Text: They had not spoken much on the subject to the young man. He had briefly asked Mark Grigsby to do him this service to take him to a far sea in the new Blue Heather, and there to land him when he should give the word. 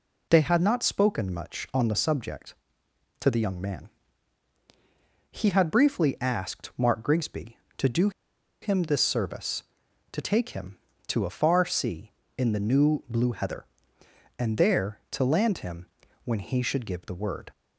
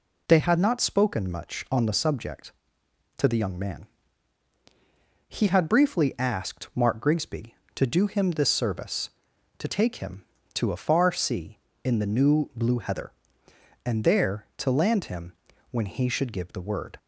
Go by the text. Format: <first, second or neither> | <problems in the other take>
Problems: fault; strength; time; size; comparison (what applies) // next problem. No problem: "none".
second | pauses between "do" and "him"; noticeable; at 8.0 s; 0.52 s long // pauses between "him" and "when"; slight; at 15.8 s; 0.36 s long; slight in the second